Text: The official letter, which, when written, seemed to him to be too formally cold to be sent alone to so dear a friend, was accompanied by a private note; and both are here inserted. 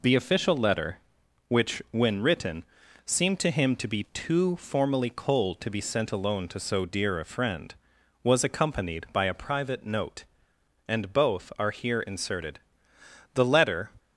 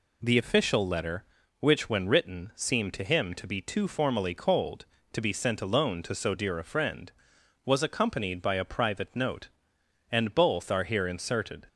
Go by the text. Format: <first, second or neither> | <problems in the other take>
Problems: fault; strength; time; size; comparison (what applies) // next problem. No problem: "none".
second | goes on to say "The letter"; from 13.3 s on; 0.56 s long